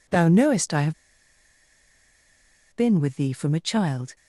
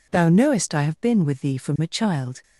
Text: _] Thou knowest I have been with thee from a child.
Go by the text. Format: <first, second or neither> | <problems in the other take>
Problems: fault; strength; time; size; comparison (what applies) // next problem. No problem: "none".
second | pauses between "have" and "been"; strong; at 0.9 s; 1.8 s long